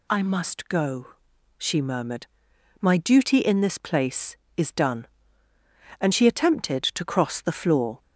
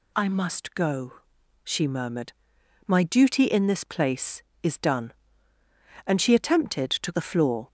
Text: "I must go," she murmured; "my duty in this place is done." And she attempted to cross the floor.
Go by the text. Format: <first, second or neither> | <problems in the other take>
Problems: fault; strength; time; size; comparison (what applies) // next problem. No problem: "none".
first | skips "cross"; at 7.1 s